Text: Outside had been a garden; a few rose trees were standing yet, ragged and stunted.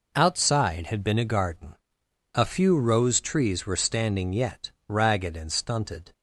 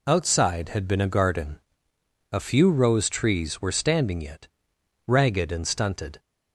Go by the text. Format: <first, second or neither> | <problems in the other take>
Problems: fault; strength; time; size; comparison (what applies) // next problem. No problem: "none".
neither | none